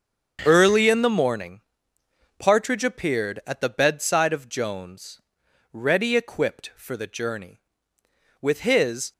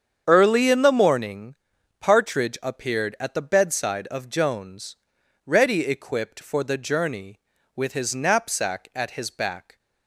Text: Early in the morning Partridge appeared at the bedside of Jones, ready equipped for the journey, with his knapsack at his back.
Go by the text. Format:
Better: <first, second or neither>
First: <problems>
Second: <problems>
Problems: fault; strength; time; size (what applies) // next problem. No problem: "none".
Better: second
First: starts louder than the rest; strong; until 1.4 s; 7 dB // pauses between "morning" and "Partridge"; noticeable; at 1.5 s; 0.78 s long // stops before "knapsack at his back"; at 9.1 s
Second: starts louder than the rest; strong; until 1.2 s; 7.5 dB // pauses between "morning" and "Partridge"; at 1.5 s; 0.44 s long